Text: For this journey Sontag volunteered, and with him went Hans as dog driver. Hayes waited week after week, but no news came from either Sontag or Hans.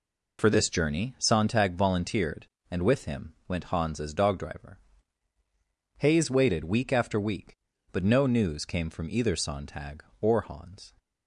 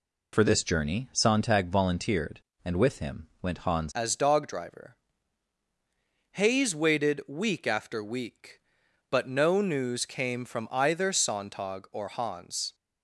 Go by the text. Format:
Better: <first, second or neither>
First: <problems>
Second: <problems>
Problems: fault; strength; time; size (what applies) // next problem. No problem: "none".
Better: first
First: none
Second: changes voice at "as"; from 3.9 s on; 8.8 s long